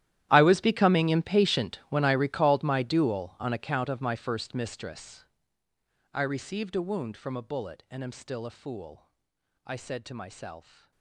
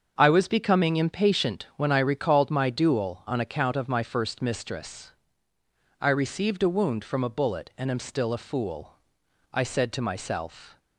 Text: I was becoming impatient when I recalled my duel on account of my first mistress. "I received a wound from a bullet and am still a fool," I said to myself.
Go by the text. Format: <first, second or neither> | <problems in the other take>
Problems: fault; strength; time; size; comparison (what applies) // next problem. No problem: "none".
second | gets quieter; strong; throughout; 20 dB // starts louder than the rest; strong; until 1.3 s; 12.5 dB; also in the second